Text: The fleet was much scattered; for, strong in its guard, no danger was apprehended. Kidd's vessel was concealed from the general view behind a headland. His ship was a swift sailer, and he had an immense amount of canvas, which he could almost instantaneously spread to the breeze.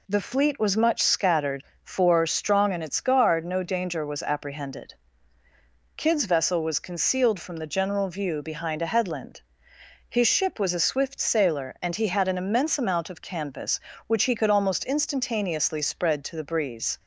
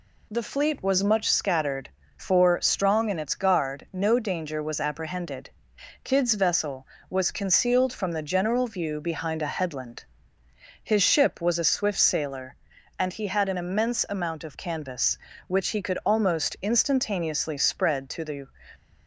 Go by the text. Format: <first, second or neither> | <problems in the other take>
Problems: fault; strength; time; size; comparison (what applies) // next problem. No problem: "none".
first | stops before "breeze"; at 18.7 s